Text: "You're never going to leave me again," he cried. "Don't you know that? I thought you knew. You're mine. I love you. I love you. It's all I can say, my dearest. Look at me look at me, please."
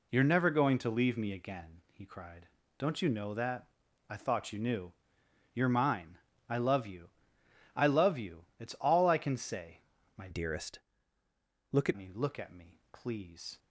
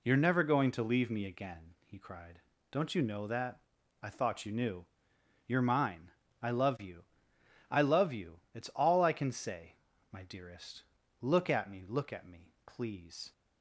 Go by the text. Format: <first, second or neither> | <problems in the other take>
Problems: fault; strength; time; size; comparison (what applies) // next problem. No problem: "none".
second | changes voice from "dearest" to "at"; from 10.3 to 11.9 s; 1.6 s long